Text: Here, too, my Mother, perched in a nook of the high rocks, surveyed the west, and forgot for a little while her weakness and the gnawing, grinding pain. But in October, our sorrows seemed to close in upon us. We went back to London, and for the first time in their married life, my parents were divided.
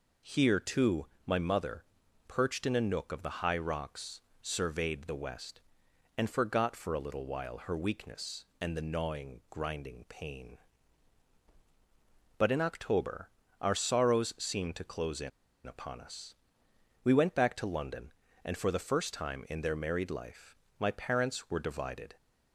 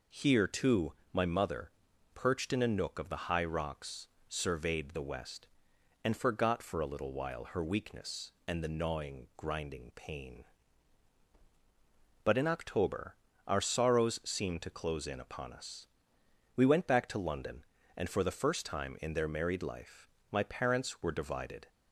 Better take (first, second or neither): second